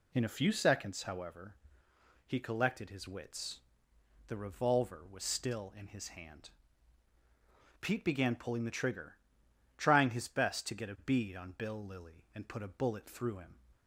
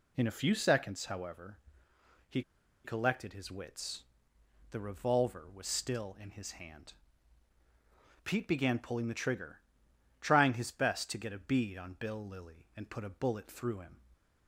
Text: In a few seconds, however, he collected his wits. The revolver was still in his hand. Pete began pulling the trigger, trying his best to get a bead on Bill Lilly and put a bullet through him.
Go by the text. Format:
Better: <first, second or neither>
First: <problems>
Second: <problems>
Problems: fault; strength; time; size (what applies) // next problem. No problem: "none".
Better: first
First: none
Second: pauses between "he" and "collected"; at 2.4 s; 0.43 s long